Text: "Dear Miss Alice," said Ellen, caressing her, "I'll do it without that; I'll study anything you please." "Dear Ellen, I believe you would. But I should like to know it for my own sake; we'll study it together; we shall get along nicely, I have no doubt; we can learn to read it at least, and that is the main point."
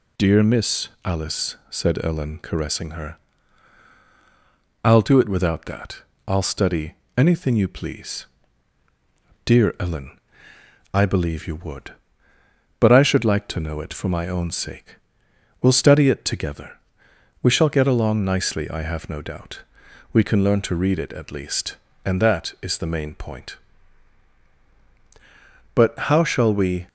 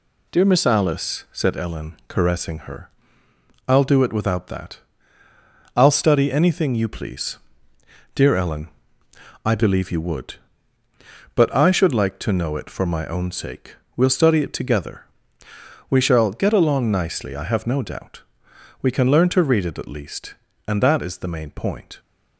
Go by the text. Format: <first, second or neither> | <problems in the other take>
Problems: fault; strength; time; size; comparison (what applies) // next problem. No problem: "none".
second | pauses between "Miss" and "Alice"; slight; at 0.8 s; 0.16 s long // pauses between "study" and "anything"; slight; at 6.9 s; 0.24 s long // goes on to say "But how shall we"; noticeable; from 25.7 s on; 1.1 s long